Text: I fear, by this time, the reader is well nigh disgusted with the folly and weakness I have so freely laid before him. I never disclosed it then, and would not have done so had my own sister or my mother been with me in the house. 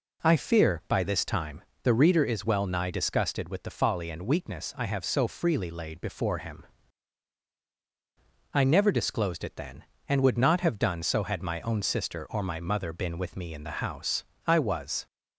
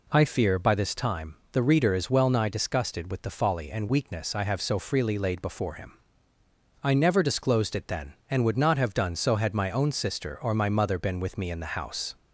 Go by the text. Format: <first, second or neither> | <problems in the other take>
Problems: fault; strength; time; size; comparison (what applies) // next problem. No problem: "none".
second | goes on to say "I was"; from 14.4 s on; 0.60 s long